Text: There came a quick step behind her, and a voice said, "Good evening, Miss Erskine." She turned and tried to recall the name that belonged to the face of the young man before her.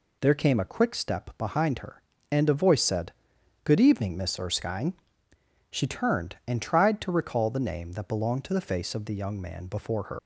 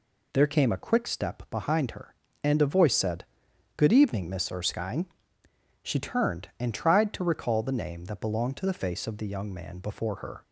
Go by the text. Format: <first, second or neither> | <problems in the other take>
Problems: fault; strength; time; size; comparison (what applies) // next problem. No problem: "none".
second | leaves "her" unfinished; at 10.1 s; 115 ms